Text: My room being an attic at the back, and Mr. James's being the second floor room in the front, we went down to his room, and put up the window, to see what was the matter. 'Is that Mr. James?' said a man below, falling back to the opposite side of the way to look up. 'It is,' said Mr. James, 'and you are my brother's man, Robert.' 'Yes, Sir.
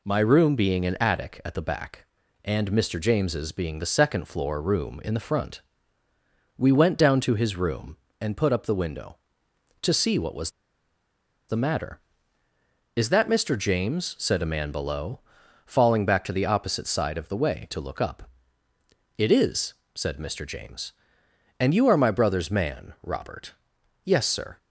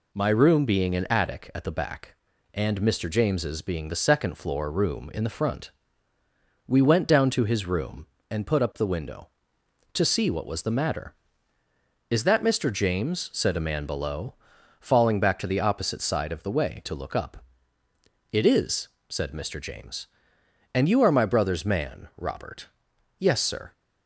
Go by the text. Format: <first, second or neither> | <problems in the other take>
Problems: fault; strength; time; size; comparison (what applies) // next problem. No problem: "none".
second | pauses between "was" and "the"; at 10.5 s; 0.98 s long